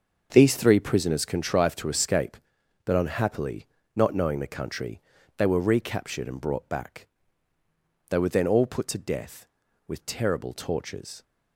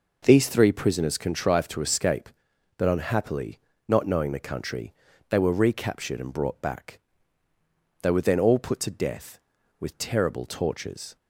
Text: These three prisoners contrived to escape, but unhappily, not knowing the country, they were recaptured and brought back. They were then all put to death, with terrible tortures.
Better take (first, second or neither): second